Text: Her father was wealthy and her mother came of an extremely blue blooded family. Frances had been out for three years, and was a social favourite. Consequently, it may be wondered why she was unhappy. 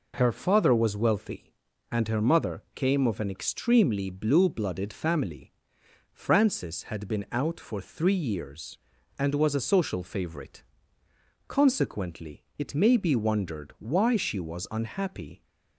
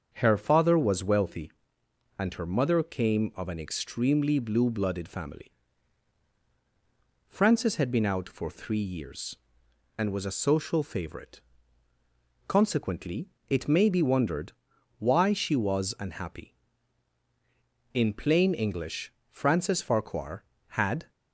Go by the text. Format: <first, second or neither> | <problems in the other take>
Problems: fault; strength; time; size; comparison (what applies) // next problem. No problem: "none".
first | starts louder than the rest; until 1.1 s; 7 dB // pauses between "wondered" and "why"; noticeable; at 14.5 s; 0.48 s long // goes on to say "In plain English Frances Farquhar had"; strong; from 17.9 s on; 3.1 s long